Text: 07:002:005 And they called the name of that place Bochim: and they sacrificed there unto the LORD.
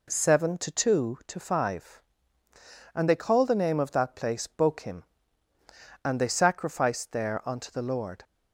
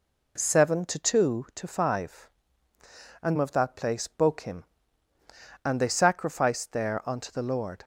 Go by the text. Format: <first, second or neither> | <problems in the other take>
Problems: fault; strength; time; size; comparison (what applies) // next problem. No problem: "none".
first | skips "they called the name"; at 3.3 s